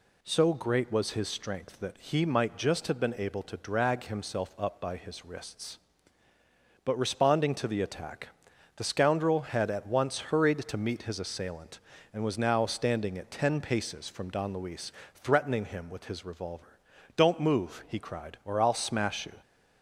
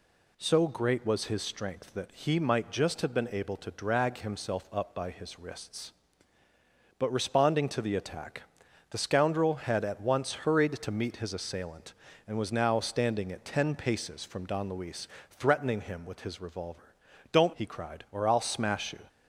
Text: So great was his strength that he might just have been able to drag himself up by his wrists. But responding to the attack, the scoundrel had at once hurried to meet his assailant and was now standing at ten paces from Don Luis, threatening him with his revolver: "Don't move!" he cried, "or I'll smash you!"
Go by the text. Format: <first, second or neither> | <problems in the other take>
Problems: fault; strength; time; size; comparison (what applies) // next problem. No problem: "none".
first | skips "move"; at 17.5 s